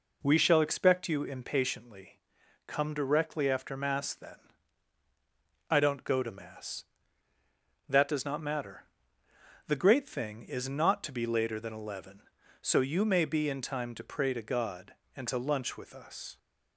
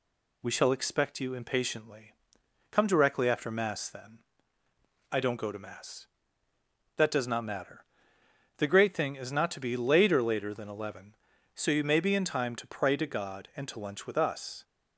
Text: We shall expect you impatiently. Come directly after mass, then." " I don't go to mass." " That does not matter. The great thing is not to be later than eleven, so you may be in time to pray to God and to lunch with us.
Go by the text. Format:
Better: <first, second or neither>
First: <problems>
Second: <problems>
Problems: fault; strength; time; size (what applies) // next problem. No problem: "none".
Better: first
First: none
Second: says "later" twice; at 10.2 s